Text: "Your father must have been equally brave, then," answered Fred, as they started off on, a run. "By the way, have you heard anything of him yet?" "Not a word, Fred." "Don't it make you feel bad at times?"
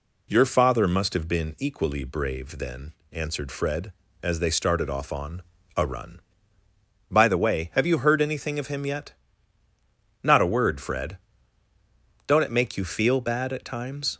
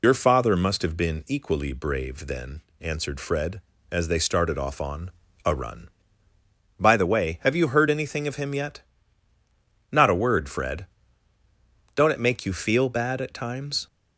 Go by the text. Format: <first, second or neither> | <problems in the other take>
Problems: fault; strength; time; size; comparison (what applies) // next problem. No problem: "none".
first | loses the start of "Your"; at 0.0 s; 70 ms